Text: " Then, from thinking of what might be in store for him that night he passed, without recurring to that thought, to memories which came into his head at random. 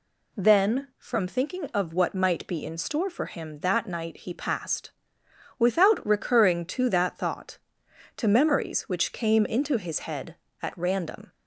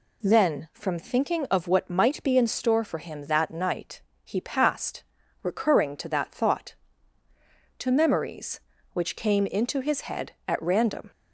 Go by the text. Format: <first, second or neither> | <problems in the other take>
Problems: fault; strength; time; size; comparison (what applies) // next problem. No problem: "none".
first | pauses between "night" and "he"; slight; at 4.0 s; 0.22 s long // skips "without"; at 5.2 s